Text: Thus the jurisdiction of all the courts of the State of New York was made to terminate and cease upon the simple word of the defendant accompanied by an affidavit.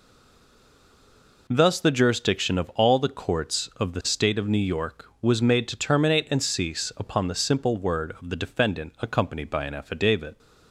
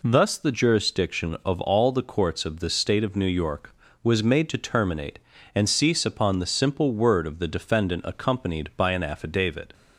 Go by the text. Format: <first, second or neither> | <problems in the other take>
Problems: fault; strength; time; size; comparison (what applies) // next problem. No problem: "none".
second | stays silent before the first word; noticeable; until 1.4 s; 1.4 s long